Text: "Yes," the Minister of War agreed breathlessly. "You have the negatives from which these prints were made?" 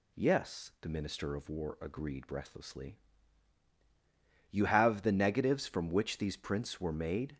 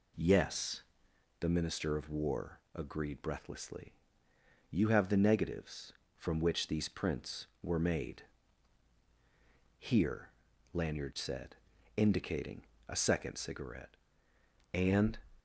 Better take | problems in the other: first | pauses between "War" and "agreed"; slight; at 2.5 s; 0.16 s long // goes on to say "Here Lanyard said indicating a second cigarette And"; strong; from 9.7 s on; 5.3 s long

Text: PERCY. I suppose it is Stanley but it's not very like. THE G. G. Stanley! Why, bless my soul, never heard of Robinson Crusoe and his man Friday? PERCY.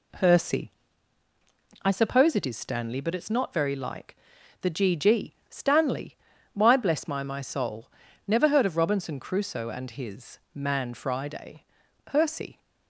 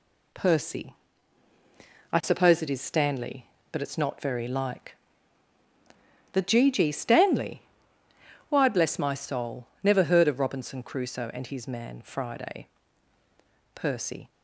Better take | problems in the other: second | pauses between "G" and "Stanley"; slight; at 5.3 s; 0.16 s long // says "my" twice; at 7.2 s // pauses between "his" and "man"; slight; at 10.3 s; 0.16 s long

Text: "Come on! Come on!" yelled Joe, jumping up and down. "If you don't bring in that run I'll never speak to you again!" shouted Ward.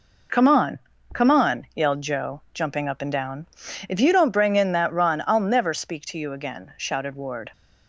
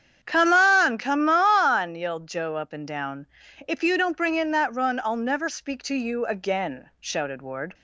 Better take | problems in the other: first | starts louder than the rest; strong; until 1.2 s; 8.5 dB // skips "jumping"; at 2.5 s

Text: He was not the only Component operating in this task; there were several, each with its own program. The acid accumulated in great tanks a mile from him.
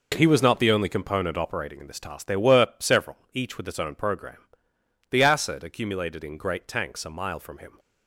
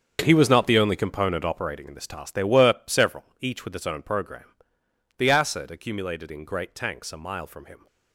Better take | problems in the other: first | gets quieter; strong; throughout; 14 dB

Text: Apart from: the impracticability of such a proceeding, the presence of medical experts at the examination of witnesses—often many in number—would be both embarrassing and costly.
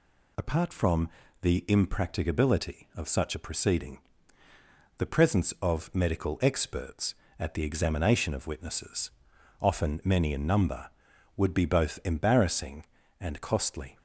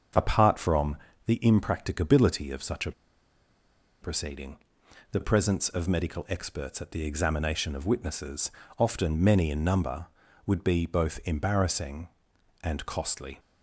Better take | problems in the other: first | starts louder than the rest; until 1.4 s; 7 dB // pauses between "a" and "proceeding"; at 2.9 s; 1.0 s long

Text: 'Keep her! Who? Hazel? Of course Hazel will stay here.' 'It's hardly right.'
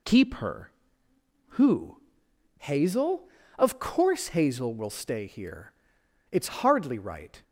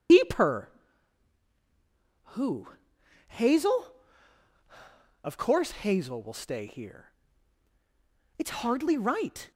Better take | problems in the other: first | loses the start of "Keep"; at 0.0 s; 145 ms

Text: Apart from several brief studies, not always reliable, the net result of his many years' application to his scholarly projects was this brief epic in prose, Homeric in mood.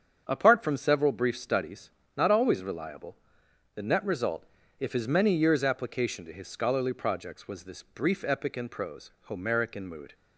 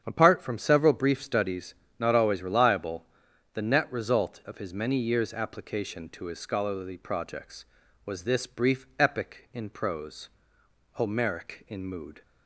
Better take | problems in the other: second | starts louder than the rest; strong; until 1.2 s; 7.5 dB; strong in the second // says "if" for "of"; at 4.7 s

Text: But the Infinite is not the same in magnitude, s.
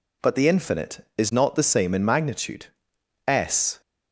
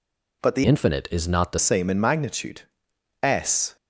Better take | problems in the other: first | changes voice from "Infinite" to "the"; from 0.6 to 1.5 s; 0.9 s long

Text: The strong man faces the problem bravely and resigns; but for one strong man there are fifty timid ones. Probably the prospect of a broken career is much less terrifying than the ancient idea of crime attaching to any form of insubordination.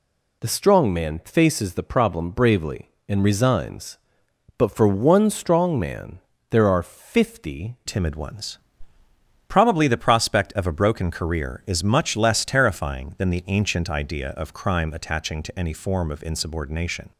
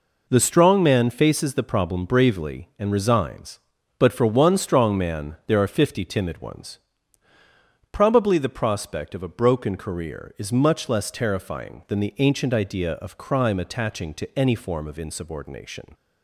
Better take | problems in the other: second | pauses between "man" and "there"; slight; at 6.1 s; 0.30 s long // changes voice at "timid"; from 7.8 s on; 9.2 s long

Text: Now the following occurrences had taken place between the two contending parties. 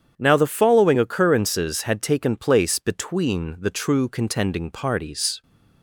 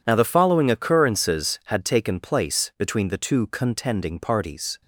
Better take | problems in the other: second | starts louder than the rest; strong; until 1.1 s; 8.5 dB // says "true" for "two"; at 3.7 s

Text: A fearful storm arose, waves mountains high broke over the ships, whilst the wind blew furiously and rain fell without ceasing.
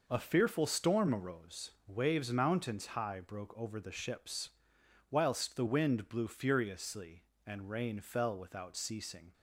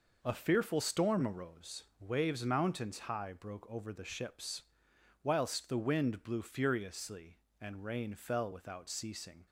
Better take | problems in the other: neither | none

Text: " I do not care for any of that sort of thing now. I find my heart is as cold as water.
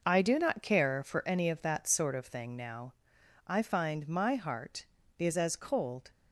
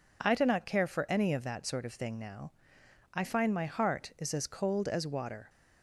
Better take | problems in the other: second | stops before "as water"; at 6.1 s

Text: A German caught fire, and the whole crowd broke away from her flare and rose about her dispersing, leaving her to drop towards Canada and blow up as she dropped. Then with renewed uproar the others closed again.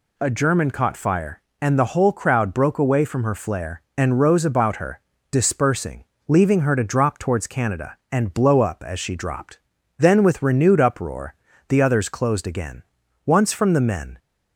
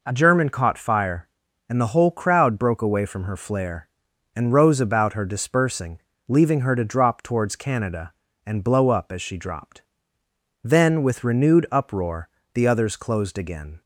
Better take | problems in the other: second | pauses between "her" and "dispersing"; slight; at 5.0 s; 0.30 s long // pauses between "uproar" and "the"; slight; at 11.3 s; 0.34 s long; slight in the second // goes on to say "Once from the men"; noticeable; from 13.2 s on; 0.92 s long

